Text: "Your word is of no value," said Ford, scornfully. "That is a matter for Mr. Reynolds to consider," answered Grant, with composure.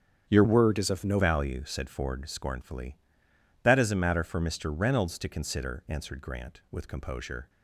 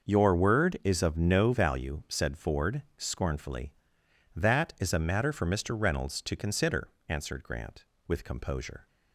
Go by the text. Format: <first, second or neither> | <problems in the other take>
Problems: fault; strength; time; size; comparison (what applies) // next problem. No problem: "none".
second | starts louder than the rest; strong; until 1.3 s; 8.5 dB // changes voice from "word" to "no"; from 0.4 to 1.1 s; 0.7 s long